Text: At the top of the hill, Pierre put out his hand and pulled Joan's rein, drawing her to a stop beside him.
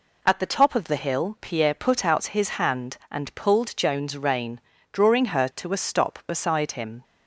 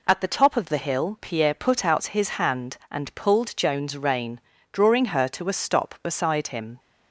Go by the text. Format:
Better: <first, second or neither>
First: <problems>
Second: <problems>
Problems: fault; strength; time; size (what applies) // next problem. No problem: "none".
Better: neither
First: none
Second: none